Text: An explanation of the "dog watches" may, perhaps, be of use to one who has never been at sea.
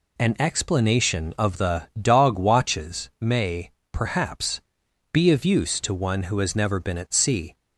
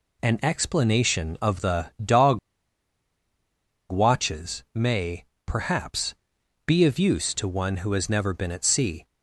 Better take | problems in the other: first | pauses between "dog" and "watches"; strong; at 2.3 s; 1.5 s long

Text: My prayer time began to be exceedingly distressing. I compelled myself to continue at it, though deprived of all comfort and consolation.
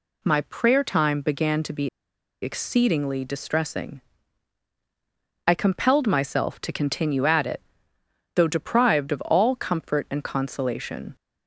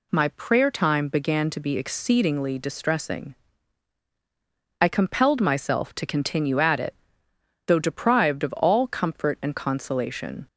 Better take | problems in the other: second | pauses between "be" and "exceedingly"; noticeable; at 1.8 s; 0.54 s long

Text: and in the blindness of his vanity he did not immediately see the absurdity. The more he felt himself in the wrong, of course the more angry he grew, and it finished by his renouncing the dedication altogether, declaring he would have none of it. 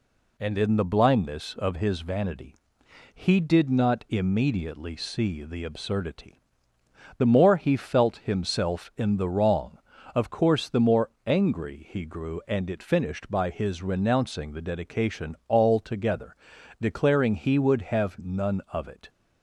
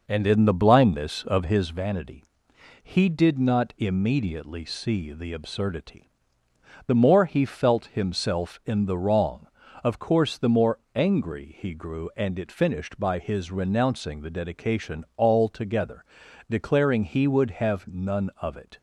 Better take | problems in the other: first | starts louder than the rest; noticeable; until 1.8 s; 5.5 dB // pauses between "vanity" and "he"; noticeable; at 2.2 s; 0.58 s long; noticeable in the first // pauses between "more" and "angry"; slight; at 10.7 s; 0.16 s long; slight in the first

